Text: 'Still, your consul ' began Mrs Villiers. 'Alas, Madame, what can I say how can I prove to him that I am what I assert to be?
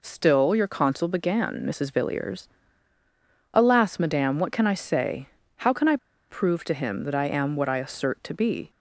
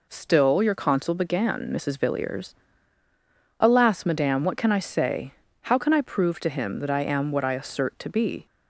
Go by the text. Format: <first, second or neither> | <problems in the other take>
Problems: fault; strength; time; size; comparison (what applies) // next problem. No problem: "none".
second | pauses between "say" and "how"; slight; at 5.2 s; 0.30 s long; slight in the second // pauses between "I" and "prove"; slight; at 5.9 s; 0.32 s long